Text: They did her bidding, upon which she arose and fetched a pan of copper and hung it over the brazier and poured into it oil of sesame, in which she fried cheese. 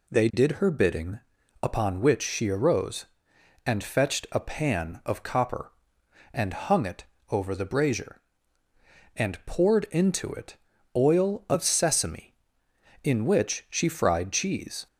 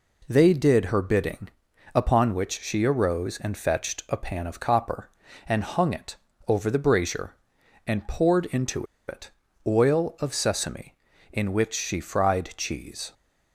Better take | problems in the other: first | pauses between "it" and "over"; slight; at 6.1 s; 0.32 s long; slight in the first // pauses between "into" and "it"; slight; at 8.8 s; 0.22 s long // pauses between "it" and "oil"; slight; at 9.3 s; 0.34 s long; also in the first

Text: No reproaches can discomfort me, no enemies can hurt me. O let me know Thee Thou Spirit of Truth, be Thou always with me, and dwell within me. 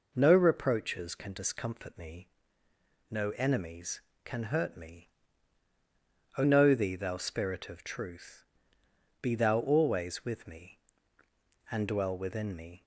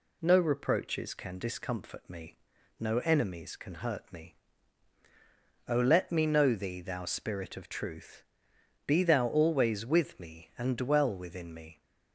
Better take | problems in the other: second | skips "let me"; at 6.4 s

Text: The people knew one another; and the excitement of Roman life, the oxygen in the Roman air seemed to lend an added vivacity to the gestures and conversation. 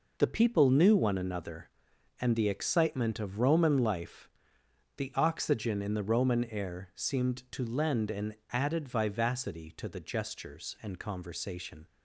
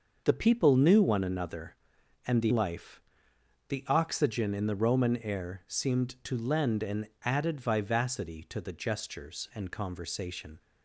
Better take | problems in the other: first | starts louder than the rest; noticeable; until 1.2 s; 6 dB // skips "excitement of Roman"; at 2.5 s // pauses between "an" and "added"; slight; at 7.0 s; 0.18 s long; slight in the first

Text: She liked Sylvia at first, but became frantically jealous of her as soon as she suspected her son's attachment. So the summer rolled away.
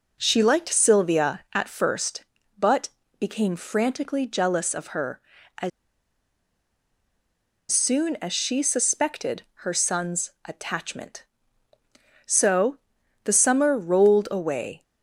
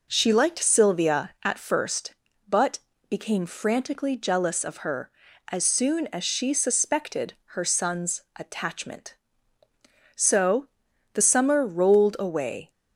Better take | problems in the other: second | pauses between "but" and "became"; slight; at 2.8 s; 0.32 s long; slight in the second // pauses between "as" and "soon"; strong; at 5.7 s; 2.0 s long // pauses between "suspected" and "her"; slight; at 9.4 s; 0.18 s long; slight in the second // pauses between "So" and "the"; at 12.7 s; 0.44 s long; also in the second

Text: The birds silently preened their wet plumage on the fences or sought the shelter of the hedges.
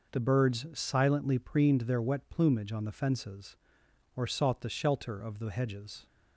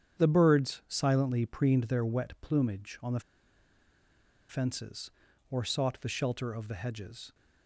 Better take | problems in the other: first | starts louder than the rest; strong; until 1.2 s; 8.5 dB // pauses between "the" and "fences"; strong; at 3.1 s; 1.2 s long

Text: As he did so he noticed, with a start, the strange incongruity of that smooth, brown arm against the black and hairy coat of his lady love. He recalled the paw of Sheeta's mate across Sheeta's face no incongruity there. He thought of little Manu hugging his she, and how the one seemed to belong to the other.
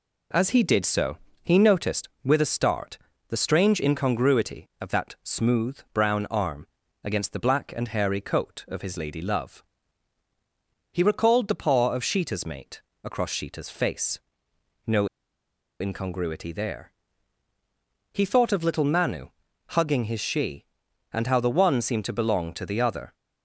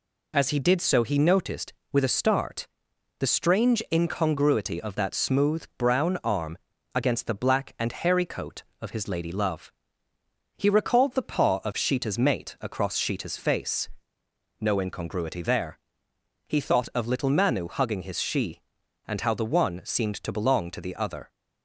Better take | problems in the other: second | pauses between "so" and "he"; slight; at 1.1 s; 0.26 s long // pauses between "arm" and "against"; slight; at 6.6 s; 0.36 s long; slight in the second // pauses between "mate" and "across"; slight; at 12.7 s; 0.24 s long // pauses between "face" and "no"; noticeable; at 14.1 s; 0.64 s long; noticeable in the second // pauses between "no" and "incongruity"; noticeable; at 15.0 s; 0.72 s long // pauses between "Manu" and "hugging"; at 19.2 s; 0.40 s long

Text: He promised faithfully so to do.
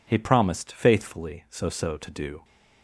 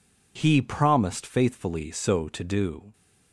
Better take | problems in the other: second | says "so" twice; at 1.6 s

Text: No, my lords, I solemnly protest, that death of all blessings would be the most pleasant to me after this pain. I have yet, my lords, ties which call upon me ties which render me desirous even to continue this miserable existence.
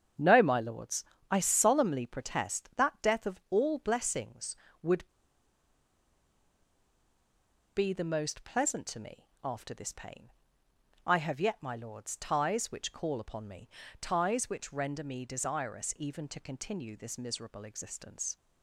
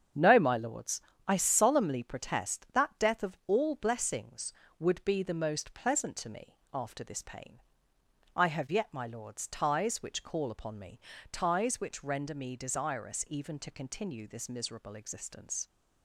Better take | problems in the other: second | starts louder than the rest; strong; until 1.4 s; 7.5 dB; strong in the second // pauses between "would" and "be"; strong; at 5.0 s; 2.6 s long // pauses between "me" and "after"; slight; at 9.2 s; 0.16 s long; slight in the second // pauses between "me" and "ties"; slight; at 13.6 s; 0.32 s long; slight in the second

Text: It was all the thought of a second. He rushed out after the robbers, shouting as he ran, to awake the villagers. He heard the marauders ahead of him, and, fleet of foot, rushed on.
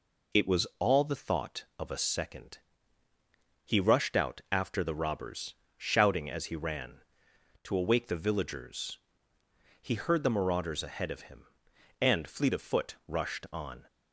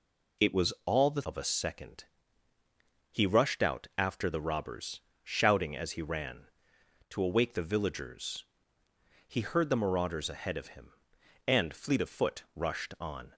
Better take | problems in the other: first | skips "thought"; at 1.2 s

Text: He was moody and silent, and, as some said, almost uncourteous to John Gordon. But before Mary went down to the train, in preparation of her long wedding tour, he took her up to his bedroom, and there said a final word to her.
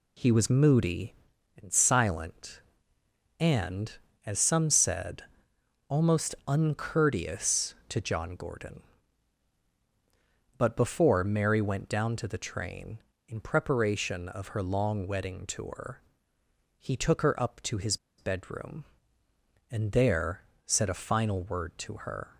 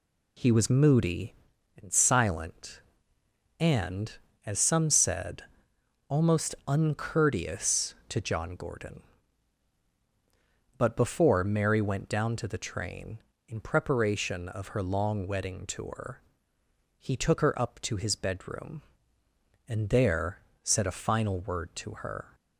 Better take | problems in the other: second | pauses between "his" and "bedroom"; slight; at 17.9 s; 0.22 s long // pauses between "there" and "said"; slight; at 20.4 s; 0.24 s long; slight in the second

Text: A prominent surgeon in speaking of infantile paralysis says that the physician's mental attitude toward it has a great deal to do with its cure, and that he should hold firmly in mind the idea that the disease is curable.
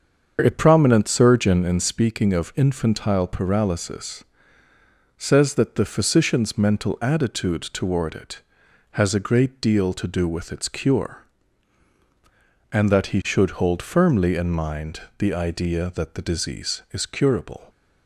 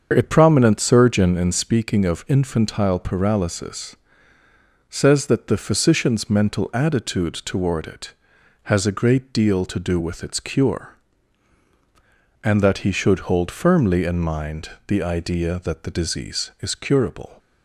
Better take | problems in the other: neither | starts louder than the rest; the same in both // pauses between "paralysis" and "says"; noticeable; the same in both // pauses between "mind" and "the"; slight; the same in both

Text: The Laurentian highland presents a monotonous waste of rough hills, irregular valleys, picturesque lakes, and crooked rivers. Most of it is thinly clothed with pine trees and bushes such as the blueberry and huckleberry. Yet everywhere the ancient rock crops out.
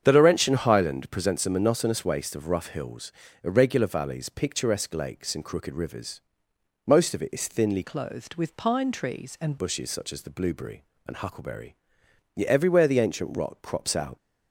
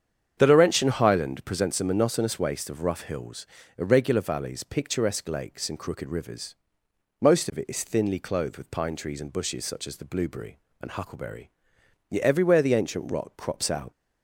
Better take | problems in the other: second | starts louder than the rest; strong; until 1.0 s; 8 dB; strong in the second // changes voice from "clothed" to "and"; from 7.8 to 9.5 s; 1.7 s long

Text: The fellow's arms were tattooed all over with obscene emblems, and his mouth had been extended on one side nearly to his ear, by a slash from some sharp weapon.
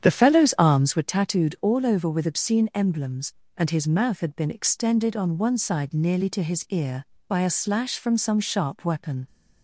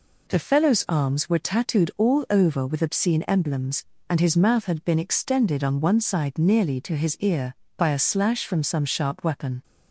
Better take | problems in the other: second | starts louder than the rest; strong; until 1.1 s; 8.5 dB

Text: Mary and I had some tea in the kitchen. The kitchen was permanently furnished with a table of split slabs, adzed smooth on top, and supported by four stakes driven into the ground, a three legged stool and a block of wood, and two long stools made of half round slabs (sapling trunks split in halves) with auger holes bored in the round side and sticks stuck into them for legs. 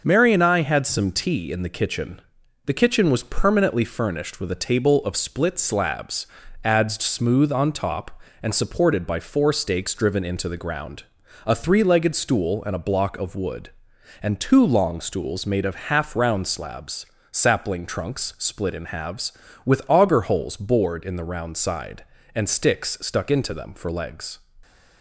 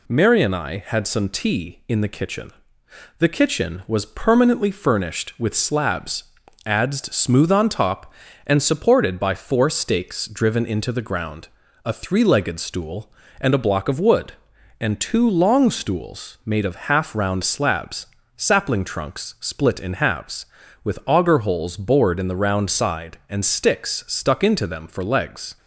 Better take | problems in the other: first | skips "a table of split"; at 5.5 s

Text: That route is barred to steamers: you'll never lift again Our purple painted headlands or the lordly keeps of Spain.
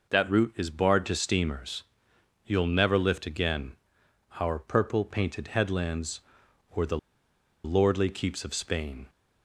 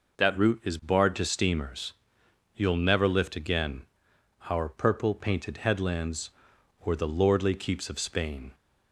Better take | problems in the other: second | pauses between "again" and "Our"; noticeable; at 3.7 s; 0.60 s long; noticeable in the second // pauses between "the" and "lordly"; noticeable; at 6.9 s; 0.66 s long

